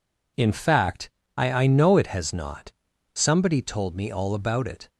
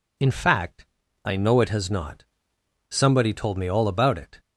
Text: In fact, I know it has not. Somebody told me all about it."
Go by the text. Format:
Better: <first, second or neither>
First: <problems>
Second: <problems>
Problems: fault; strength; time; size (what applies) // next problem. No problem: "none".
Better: second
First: says "I" twice; at 1.5 s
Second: none